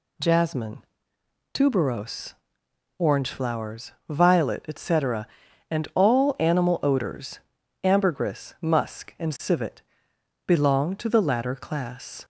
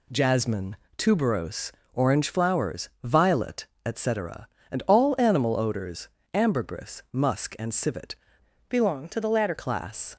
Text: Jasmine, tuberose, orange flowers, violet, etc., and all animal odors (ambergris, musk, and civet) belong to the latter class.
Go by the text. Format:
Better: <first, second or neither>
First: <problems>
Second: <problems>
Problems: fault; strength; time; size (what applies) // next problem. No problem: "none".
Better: first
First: none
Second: changes voice from "belong" to "latter"; from 8.6 to 9.5 s; 0.9 s long